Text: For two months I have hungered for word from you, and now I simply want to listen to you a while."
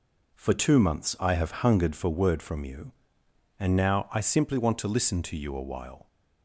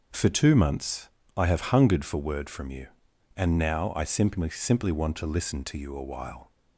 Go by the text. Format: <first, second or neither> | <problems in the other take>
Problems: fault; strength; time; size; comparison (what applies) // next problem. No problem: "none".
first | pauses between "months" and "I"; slight; at 1.0 s; 0.28 s long // says "simply" twice; at 4.4 s